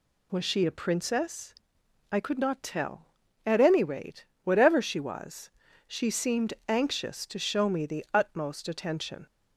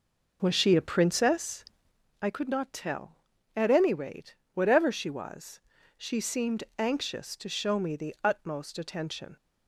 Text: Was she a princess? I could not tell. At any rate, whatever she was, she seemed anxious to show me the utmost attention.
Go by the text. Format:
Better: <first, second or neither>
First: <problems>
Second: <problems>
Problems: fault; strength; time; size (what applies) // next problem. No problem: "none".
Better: first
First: none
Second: starts louder than the rest; noticeable; until 2.1 s; 5 dB